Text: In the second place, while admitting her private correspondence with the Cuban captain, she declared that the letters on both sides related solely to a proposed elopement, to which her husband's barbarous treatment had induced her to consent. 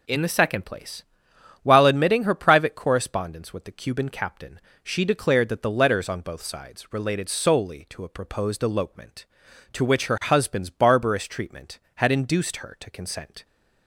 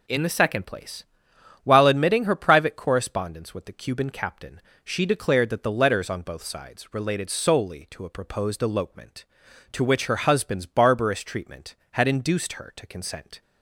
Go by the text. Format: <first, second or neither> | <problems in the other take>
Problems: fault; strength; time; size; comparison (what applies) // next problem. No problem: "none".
neither | none